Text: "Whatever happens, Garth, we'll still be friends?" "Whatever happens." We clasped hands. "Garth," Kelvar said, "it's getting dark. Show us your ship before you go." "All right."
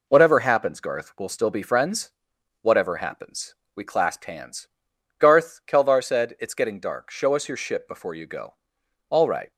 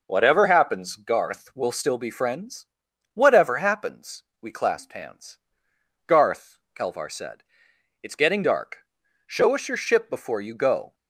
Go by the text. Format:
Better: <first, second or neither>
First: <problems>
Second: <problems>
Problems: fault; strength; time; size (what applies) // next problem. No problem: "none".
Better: first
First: none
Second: stops before "All right"; at 10.9 s